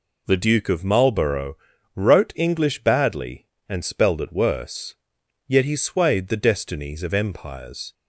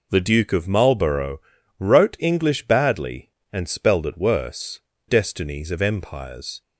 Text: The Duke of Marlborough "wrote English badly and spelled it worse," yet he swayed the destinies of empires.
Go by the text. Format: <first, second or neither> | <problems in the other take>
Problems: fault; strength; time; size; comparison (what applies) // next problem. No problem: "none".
first | pauses between "Marlborough" and "wrote"; at 1.3 s; 0.40 s long; also in the first // skips "yet he swayed the"; at 4.9 s